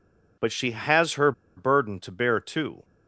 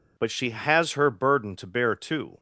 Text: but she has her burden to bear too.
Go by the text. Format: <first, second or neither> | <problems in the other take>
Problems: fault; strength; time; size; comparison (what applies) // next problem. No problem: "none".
second | pauses between "her" and "burden"; slight; at 1.3 s; 0.24 s long